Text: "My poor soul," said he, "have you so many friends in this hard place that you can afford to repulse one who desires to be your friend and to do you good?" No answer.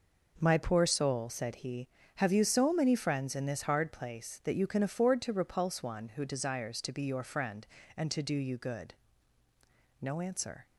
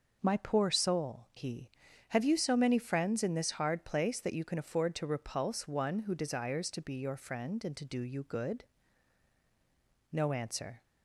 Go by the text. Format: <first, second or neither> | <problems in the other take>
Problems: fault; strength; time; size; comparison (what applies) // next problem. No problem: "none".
first | skips "said"; at 1.3 s